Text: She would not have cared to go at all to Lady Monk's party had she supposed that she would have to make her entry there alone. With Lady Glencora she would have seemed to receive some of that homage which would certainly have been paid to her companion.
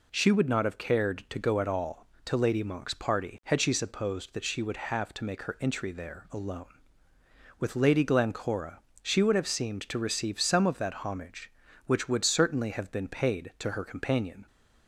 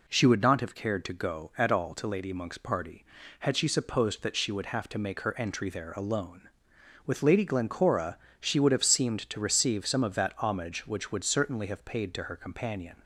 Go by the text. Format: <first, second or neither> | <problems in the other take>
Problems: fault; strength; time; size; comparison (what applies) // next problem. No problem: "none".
first | pauses between "Glencora" and "she"; slight; at 8.1 s; 0.22 s long; slight in the first // skips "been"; at 11.8 s